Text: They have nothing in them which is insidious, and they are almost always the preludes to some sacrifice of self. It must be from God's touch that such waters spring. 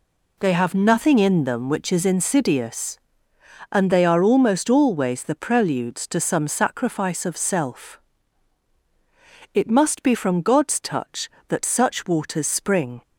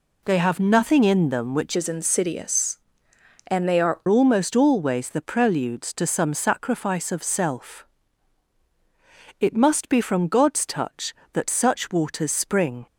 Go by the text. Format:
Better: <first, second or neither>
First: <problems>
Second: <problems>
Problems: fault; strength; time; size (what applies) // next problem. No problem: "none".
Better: first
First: none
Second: changes voice from "is" to "are"; from 1.7 to 4.0 s; 2.3 s long